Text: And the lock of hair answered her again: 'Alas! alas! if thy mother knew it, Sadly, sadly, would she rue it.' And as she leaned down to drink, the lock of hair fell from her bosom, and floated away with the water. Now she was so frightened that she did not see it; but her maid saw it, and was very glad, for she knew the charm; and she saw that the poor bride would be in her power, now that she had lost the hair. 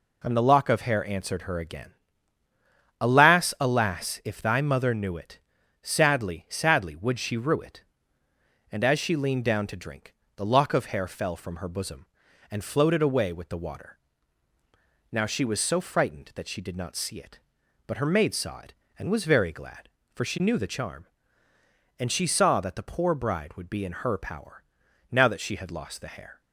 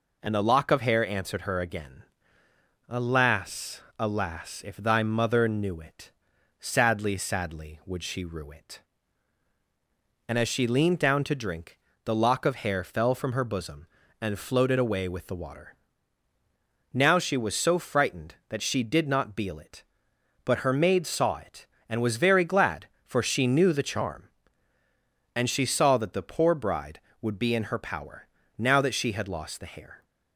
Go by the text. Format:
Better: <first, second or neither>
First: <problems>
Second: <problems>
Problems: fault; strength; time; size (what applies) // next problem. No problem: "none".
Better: first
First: none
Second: says "beel" for "see"; at 19.3 s